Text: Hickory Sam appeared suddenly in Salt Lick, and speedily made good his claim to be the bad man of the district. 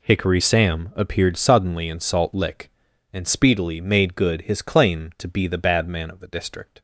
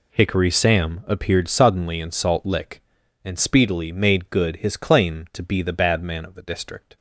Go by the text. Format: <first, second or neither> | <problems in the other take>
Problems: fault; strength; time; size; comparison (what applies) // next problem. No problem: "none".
neither | none